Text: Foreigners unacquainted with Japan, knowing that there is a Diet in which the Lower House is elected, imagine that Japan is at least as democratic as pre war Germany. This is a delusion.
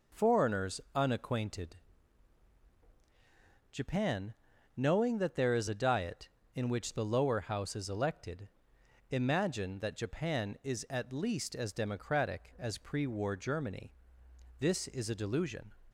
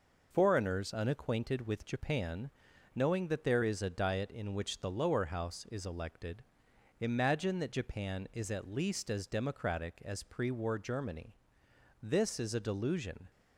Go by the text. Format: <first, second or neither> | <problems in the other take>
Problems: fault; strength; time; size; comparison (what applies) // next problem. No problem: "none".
second | skips "with"; at 2.7 s